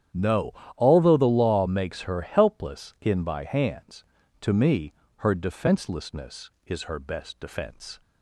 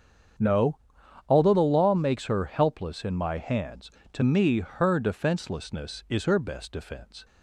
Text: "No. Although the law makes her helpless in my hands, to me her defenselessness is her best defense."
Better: second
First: starts louder than the rest; strong; until 1.3 s; 9.5 dB // says "by" for "my"; at 3.2 s // pauses between "me" and "her"; slight; at 4.9 s; 0.22 s long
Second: starts louder than the rest; strong; until 1.9 s; 8 dB

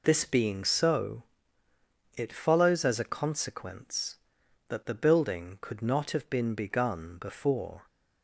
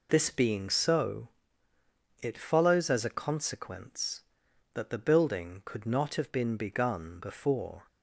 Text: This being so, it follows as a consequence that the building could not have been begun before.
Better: neither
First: none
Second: none

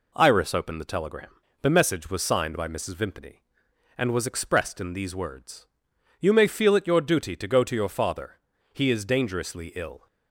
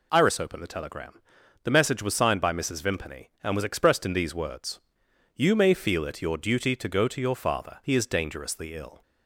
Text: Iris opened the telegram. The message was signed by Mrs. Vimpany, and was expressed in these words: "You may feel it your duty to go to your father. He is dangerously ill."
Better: neither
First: none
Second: none

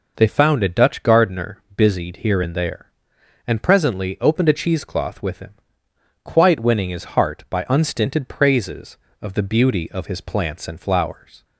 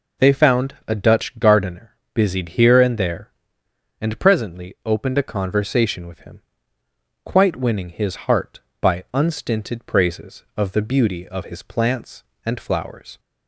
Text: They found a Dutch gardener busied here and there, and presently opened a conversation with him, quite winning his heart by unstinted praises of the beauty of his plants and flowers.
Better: second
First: pauses between "gardener" and "busied"; slight; at 1.5 s; 0.16 s long // says "cheesecloth" for "conversation"; at 4.5 s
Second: pauses between "gardener" and "busied"; slight; at 1.9 s; 0.20 s long

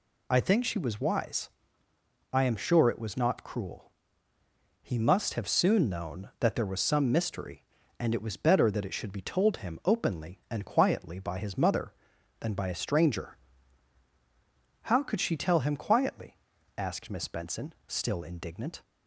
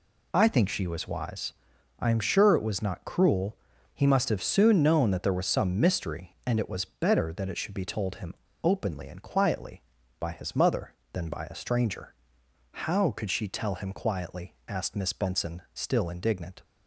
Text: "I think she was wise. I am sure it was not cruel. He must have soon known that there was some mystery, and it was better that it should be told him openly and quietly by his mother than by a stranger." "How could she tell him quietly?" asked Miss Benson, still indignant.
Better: first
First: none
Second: pauses between "him" and "openly"; slight; at 8.3 s; 0.28 s long

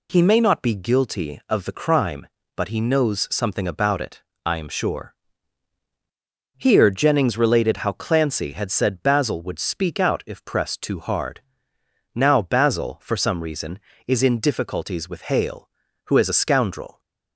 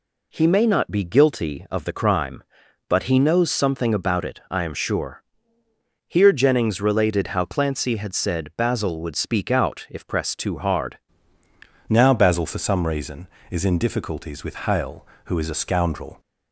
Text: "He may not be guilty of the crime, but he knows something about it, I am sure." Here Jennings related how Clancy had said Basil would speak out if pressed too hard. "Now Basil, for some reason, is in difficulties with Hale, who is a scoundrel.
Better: first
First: none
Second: changes voice at "Now"; from 11.8 s on; 4.3 s long

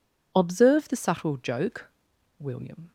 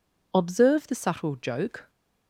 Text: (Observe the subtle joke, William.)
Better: first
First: none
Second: stops before "William"; at 1.8 s

